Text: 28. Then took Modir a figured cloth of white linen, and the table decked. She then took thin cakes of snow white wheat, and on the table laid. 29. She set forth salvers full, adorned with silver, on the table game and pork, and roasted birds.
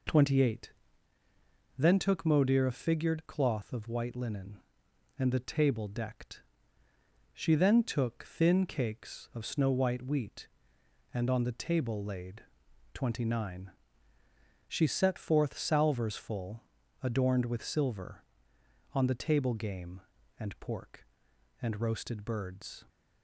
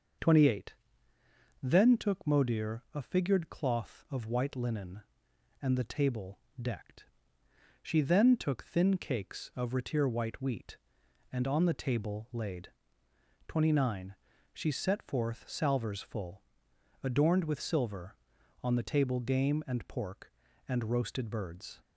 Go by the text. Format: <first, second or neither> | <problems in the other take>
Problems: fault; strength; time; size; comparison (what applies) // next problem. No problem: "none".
first | starts louder than the rest; until 2.1 s; 6.5 dB // pauses between "table" and "decked"; slight; at 6.4 s; 0.20 s long // says "retir" for "snow"; at 9.7 s